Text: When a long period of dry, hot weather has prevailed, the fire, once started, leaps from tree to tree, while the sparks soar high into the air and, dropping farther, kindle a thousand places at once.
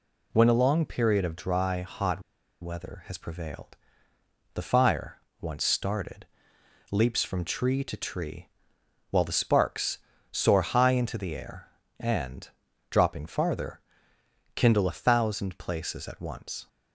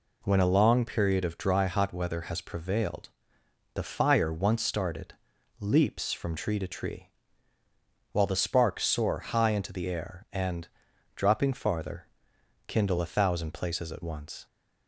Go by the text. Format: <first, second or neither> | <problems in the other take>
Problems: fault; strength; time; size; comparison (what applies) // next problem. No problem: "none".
second | pauses between "hot" and "weather"; at 2.2 s; 0.39 s long // pauses between "sparks" and "soar"; slight; at 9.9 s; 0.32 s long